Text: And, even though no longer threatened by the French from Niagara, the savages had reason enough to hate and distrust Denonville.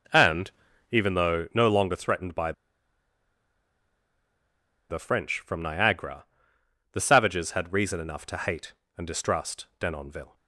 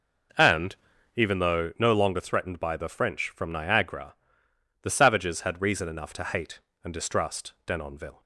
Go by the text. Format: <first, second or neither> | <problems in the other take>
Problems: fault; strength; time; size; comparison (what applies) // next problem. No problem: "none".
second | pauses between "by" and "the"; strong; at 2.5 s; 2.3 s long